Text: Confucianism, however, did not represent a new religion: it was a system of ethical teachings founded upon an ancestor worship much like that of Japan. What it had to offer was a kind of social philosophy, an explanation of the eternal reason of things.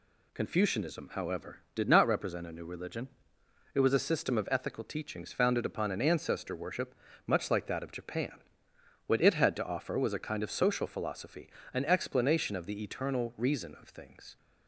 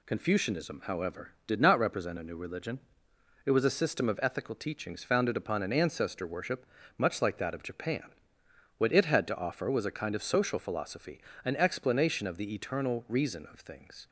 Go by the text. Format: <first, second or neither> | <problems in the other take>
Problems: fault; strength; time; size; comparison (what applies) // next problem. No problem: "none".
neither | pauses between "worship" and "much"; slight; the same in both